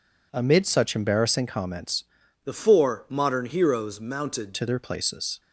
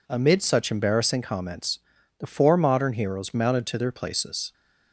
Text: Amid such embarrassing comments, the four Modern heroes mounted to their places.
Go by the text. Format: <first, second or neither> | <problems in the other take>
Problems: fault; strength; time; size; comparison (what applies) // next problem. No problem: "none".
second | changes voice from "the" to "mounted"; from 2.4 to 4.5 s; 2.1 s long